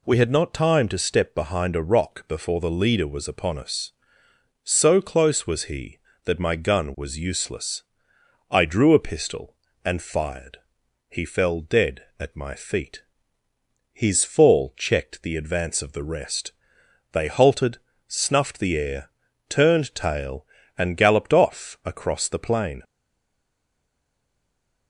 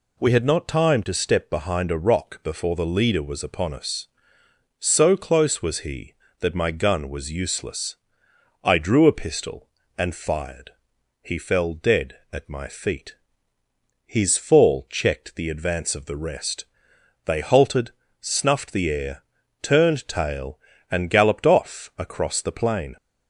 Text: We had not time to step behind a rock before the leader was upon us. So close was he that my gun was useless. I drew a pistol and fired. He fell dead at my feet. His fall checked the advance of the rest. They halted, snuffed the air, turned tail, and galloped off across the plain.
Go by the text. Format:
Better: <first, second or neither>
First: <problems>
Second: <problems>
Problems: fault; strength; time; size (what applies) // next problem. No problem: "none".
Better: second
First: stays silent after the last word; noticeable; from 22.8 s on; 2.0 s long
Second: none